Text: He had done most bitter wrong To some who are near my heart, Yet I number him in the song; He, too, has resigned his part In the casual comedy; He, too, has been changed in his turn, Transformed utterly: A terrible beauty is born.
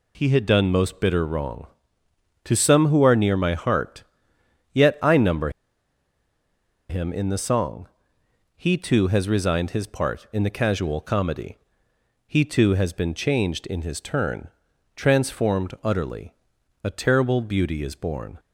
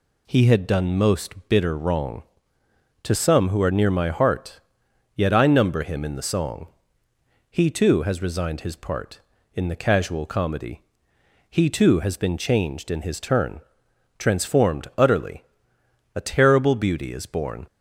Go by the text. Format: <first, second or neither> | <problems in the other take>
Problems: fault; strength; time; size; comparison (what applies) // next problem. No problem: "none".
second | pauses between "number" and "him"; strong; at 5.4 s; 1.3 s long